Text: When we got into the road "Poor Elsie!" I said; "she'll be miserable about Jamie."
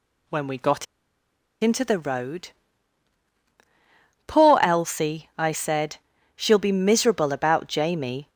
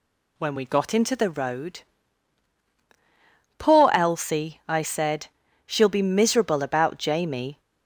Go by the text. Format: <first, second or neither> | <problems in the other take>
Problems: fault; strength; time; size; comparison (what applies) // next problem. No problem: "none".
second | pauses between "got" and "into"; noticeable; at 0.8 s; 0.76 s long // pauses between "road" and "Poor"; strong; at 2.5 s; 1.7 s long; strong in the second